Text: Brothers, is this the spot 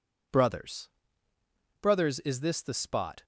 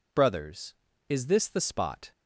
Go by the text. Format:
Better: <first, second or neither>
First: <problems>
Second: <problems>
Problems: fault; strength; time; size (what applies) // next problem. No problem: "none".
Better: second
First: says "Brothers" twice; at 1.8 s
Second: none